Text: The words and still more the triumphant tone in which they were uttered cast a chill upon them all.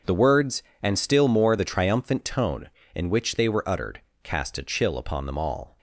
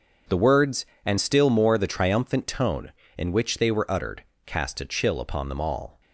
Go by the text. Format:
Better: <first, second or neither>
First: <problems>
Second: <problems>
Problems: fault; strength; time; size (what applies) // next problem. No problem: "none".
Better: neither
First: starts louder than the rest; until 1.2 s; 6.5 dB // pauses between "uttered" and "cast"; slight; at 4.0 s; 0.20 s long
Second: starts louder than the rest; until 1.5 s; 6.5 dB // pauses between "uttered" and "cast"; slight; at 4.2 s; 0.20 s long